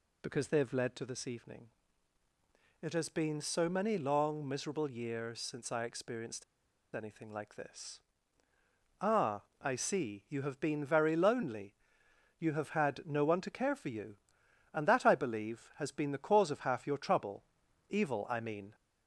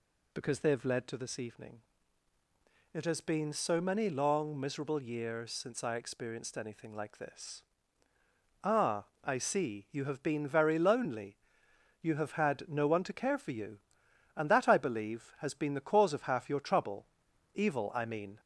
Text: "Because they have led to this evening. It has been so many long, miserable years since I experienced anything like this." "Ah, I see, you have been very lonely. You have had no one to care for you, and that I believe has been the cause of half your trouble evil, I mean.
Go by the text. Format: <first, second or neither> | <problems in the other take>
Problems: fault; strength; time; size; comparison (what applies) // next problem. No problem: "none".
second | pauses between "experienced" and "anything"; noticeable; at 6.4 s; 0.50 s long // pauses between "trouble" and "evil"; at 17.4 s; 0.44 s long; noticeable in the second